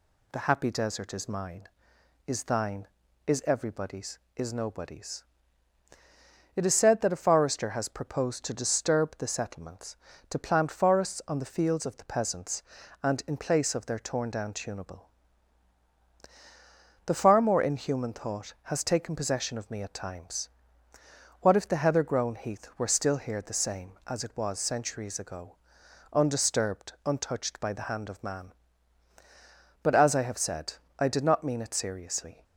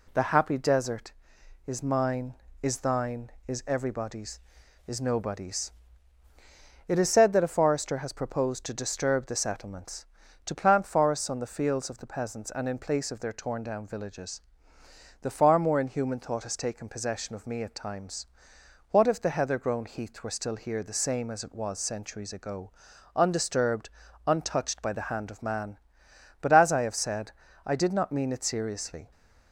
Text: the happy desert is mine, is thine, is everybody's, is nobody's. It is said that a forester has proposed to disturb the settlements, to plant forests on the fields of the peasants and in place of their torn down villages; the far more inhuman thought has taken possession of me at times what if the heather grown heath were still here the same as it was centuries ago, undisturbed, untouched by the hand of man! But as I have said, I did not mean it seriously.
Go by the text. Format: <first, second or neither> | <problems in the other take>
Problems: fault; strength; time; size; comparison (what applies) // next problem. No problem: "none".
second | says "tunable" for "villages"; at 14.5 s // pauses between "times" and "what"; noticeable; at 20.4 s; 0.92 s long; noticeable in the second